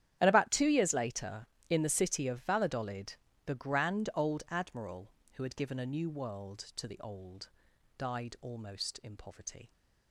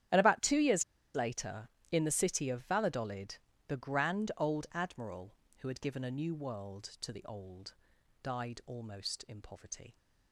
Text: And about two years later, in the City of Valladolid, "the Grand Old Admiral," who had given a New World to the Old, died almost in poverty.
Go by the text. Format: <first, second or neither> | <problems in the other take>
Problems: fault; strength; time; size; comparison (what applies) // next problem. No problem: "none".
first | starts louder than the rest; strong; until 1.4 s; 10.5 dB; strong in the first // pauses between "years" and "later"; slight; at 0.8 s; 0.31 s long